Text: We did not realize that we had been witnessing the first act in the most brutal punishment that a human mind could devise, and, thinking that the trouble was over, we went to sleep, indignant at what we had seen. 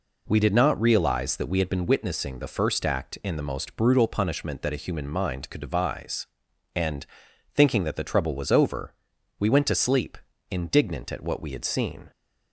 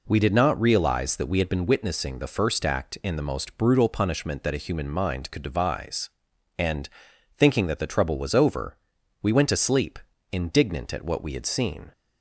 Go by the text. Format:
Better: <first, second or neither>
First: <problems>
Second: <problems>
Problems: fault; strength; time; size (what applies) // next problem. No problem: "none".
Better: neither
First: none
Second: none